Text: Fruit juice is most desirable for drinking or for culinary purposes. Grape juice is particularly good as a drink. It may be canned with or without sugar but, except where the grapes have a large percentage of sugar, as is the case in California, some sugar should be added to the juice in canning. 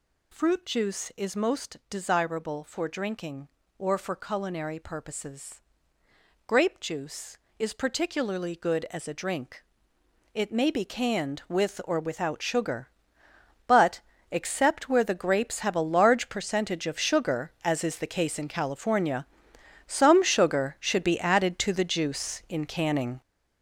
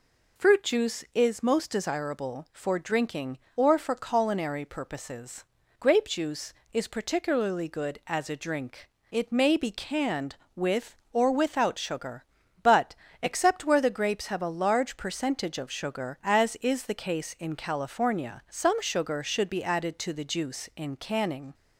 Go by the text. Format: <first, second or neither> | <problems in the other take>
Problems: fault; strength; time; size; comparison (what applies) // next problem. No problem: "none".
second | gets louder; strong; throughout; 8 dB